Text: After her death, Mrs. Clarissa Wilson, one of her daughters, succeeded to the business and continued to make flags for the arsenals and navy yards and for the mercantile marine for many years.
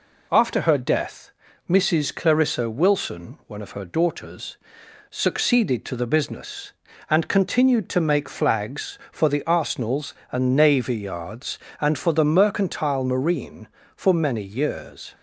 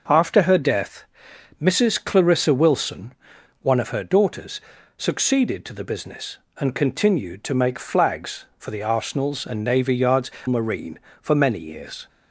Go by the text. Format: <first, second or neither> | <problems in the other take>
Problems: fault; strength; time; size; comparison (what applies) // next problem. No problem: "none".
first | skips "and for the mercantile"; at 10.3 s